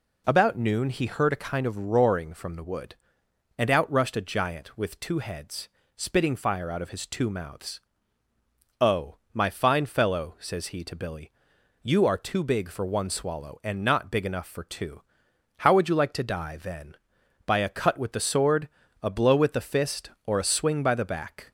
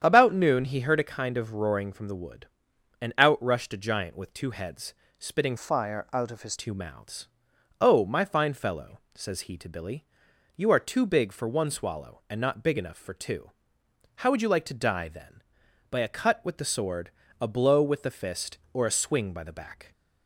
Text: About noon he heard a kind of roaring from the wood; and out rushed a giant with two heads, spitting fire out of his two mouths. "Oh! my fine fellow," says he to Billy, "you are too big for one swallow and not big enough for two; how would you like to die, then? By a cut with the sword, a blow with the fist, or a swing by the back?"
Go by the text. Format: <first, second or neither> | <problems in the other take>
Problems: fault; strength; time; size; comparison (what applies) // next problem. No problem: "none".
first | starts louder than the rest; strong; until 1.0 s; 8.5 dB // changes voice from "fire" to "his"; from 5.5 to 6.5 s; 1.0 s long